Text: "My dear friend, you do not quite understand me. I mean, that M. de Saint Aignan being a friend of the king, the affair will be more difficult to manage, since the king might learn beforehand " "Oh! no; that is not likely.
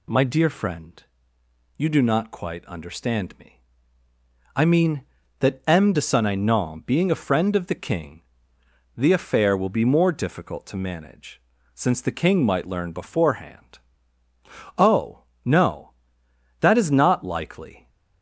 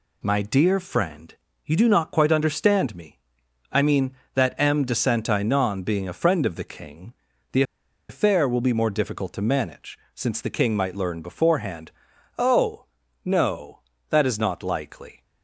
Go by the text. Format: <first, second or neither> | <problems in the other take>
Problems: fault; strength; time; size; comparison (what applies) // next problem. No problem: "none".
first | pauses between "the" and "affair"; noticeable; at 7.6 s; 0.47 s long